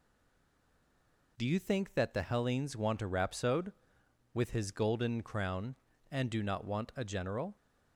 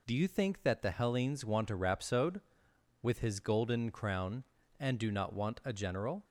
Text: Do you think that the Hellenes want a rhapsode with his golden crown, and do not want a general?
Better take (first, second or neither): second